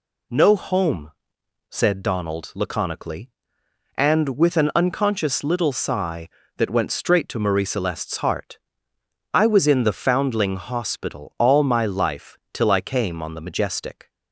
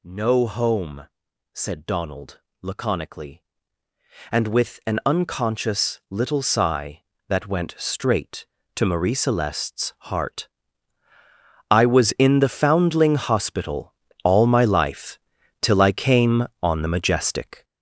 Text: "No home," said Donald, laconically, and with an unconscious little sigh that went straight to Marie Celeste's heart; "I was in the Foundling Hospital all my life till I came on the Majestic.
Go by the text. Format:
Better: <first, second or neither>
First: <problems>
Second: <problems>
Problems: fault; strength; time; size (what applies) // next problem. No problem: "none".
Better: first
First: none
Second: gets louder; strong; throughout; 7.5 dB // pauses between "Hospital" and "all"; slight; at 13.9 s; 0.30 s long // pauses between "life" and "till"; at 15.1 s; 0.44 s long